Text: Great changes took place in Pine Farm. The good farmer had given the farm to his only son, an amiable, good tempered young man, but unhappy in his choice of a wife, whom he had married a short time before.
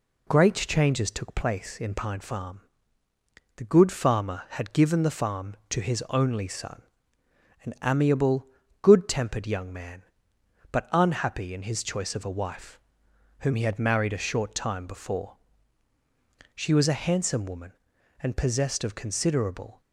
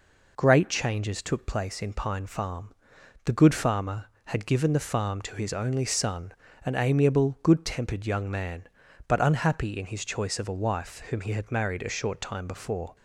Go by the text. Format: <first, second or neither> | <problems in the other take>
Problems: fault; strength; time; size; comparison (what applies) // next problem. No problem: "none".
second | goes on to say "She was a handsome woman and possessed of considerable"; strong; from 16.5 s on; 3.2 s long